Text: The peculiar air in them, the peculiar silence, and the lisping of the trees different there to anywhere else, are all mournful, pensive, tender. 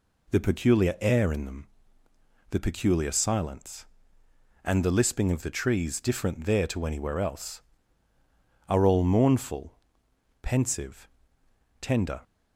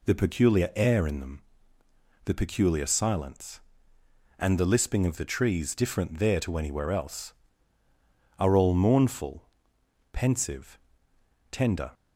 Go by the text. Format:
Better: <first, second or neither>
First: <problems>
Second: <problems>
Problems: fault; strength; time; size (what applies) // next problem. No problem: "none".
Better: neither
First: none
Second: none